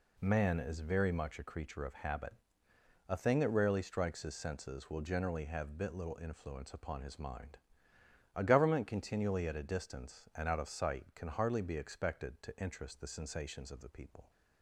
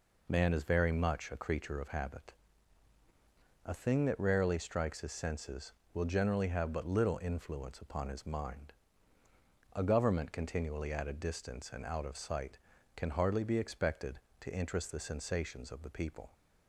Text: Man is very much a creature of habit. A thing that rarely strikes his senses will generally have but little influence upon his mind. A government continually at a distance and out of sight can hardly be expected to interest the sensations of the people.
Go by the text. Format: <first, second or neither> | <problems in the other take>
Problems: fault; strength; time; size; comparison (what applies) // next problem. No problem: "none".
second | says "bit" for "but"; at 5.7 s